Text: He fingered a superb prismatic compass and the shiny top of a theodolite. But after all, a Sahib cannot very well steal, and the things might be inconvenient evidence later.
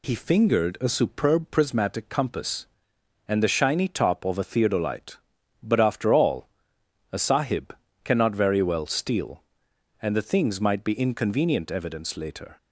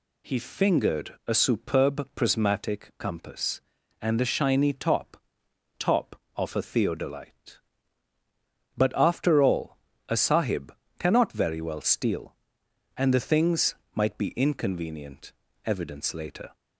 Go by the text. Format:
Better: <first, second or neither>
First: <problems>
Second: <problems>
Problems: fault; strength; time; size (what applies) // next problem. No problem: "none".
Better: first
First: pauses between "Sahib" and "cannot"; slight; at 7.7 s; 0.28 s long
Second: says "top" twice; at 5.7 s // pauses between "Sahib" and "cannot"; slight; at 10.7 s; 0.24 s long // pauses between "things" and "might"; slight; at 13.7 s; 0.18 s long // pauses between "inconvenient" and "evidence"; slight; at 15.3 s; 0.32 s long